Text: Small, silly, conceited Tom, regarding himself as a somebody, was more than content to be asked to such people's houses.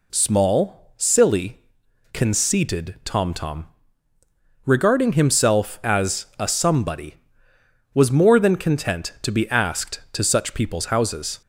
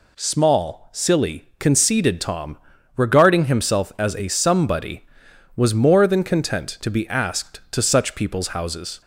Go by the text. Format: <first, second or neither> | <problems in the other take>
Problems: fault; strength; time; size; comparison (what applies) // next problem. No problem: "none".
second | says "Tom" twice; at 3.3 s